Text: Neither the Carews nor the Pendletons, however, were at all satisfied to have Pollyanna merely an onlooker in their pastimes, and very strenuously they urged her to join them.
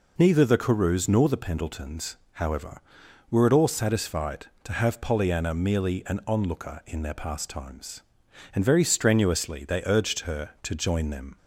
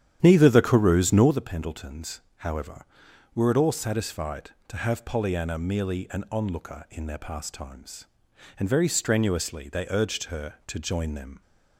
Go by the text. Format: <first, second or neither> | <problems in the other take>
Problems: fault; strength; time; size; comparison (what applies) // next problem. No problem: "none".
first | starts louder than the rest; strong; until 1.4 s; 10 dB